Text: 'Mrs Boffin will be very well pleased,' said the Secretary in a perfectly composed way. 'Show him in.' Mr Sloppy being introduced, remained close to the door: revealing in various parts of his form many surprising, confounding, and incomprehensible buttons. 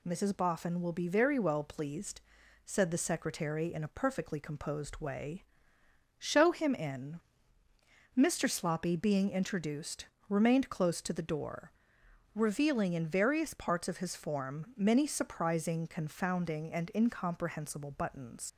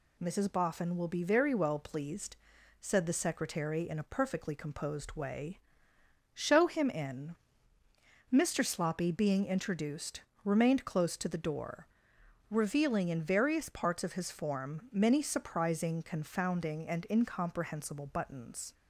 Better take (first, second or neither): second